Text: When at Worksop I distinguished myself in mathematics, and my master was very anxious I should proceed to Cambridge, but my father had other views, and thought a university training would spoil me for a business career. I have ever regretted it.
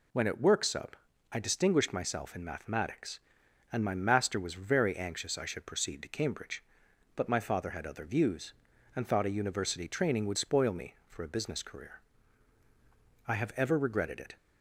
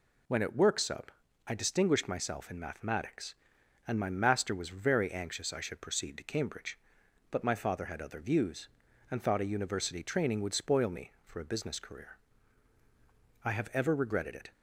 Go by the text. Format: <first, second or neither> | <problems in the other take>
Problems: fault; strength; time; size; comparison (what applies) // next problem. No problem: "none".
neither | pauses between "Worksop" and "I"; slight; the same in both